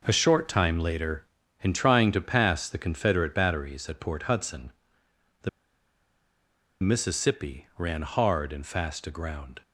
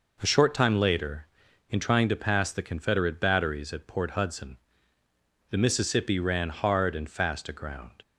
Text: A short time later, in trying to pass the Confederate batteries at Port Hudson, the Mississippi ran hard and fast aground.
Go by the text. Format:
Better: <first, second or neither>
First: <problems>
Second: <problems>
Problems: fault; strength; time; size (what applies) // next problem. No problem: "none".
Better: second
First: pauses between "the" and "Mississippi"; strong; at 5.4 s; 1.3 s long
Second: none